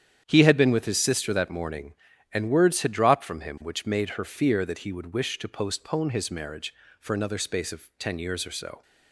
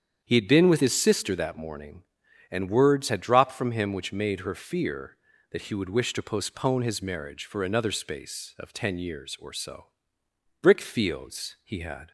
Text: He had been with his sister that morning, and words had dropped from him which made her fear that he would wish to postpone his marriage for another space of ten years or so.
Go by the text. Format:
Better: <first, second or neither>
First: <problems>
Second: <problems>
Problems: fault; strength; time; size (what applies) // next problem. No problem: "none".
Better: first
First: starts louder than the rest; strong; until 1.2 s; 9 dB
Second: starts louder than the rest; strong; until 1.2 s; 8.5 dB // goes on to say "Brick fields he had"; from 10.6 s on; 1.5 s long